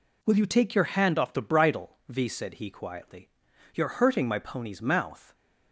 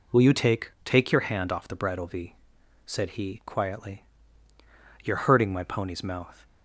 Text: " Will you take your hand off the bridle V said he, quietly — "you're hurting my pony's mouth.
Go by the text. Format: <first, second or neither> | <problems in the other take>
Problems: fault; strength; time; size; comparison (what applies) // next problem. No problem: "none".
first | says "take" twice; at 0.8 s // pauses between "V" and "said"; noticeable; at 2.3 s; 0.52 s long